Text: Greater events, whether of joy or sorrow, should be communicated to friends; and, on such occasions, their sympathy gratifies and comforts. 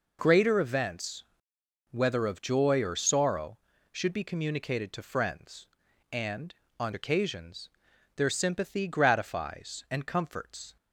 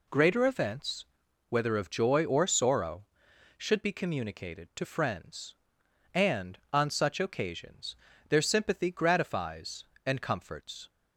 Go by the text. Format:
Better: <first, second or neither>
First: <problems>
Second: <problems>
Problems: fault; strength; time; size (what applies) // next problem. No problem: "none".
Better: second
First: skips "such"; at 6.9 s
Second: none